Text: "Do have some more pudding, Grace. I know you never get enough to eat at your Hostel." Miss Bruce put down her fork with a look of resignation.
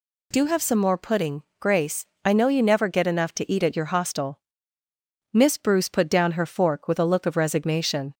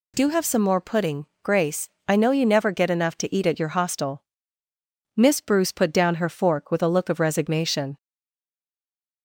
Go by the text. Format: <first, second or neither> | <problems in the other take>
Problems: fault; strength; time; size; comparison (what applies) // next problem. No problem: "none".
first | stays silent after the last word; noticeable; from 7.9 s on; 1.3 s long